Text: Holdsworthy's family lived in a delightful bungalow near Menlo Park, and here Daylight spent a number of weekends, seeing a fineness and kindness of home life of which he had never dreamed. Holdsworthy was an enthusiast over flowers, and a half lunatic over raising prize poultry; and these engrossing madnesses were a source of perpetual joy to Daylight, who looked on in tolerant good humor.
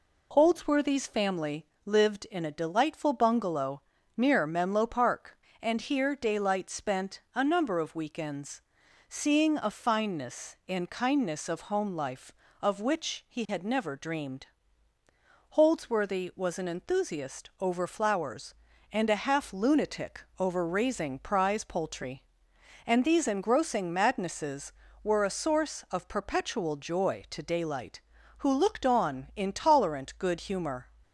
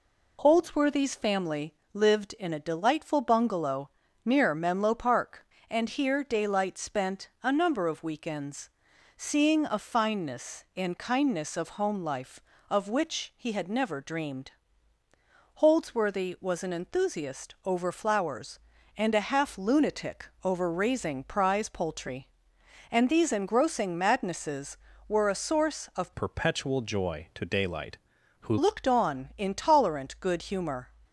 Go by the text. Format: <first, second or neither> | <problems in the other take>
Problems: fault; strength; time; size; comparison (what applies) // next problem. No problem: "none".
first | pauses between "family" and "lived"; slight; at 1.7 s; 0.18 s long; slight in the first // pauses between "bungalow" and "near"; slight; at 3.8 s; 0.34 s long; slight in the first // pauses between "lunatic" and "over"; slight; at 20.2 s; 0.16 s long; slight in the first // changes voice from "perpetual" to "who"; from 26.1 to 28.5 s; 2.4 s long